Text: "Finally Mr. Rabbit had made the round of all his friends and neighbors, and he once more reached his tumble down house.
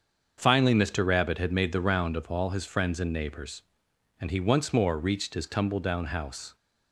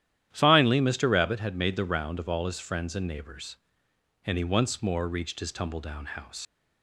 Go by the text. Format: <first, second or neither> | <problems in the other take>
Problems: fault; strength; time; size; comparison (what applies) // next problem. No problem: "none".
first | starts louder than the rest; strong; until 1.3 s; 11.5 dB; also in the first // leaves "house" unfinished; at 6.4 s; 95 ms